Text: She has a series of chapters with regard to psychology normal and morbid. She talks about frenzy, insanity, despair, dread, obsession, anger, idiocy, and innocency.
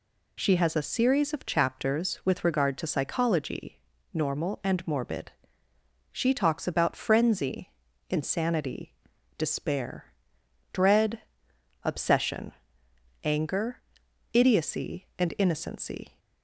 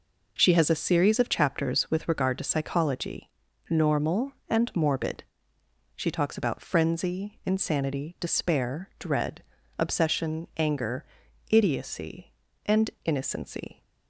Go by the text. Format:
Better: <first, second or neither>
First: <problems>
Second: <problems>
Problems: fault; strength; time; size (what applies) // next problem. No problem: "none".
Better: neither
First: pauses between "psychology" and "normal"; slight; at 3.8 s; 0.32 s long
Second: pauses between "psychology" and "normal"; at 3.3 s; 0.38 s long